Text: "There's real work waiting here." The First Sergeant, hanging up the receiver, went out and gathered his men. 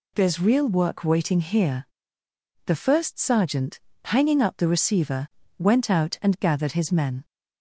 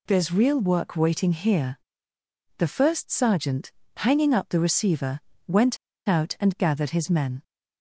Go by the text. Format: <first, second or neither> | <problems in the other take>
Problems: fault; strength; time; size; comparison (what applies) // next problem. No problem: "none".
first | pauses between "went" and "out"; slight; at 5.7 s; 0.31 s long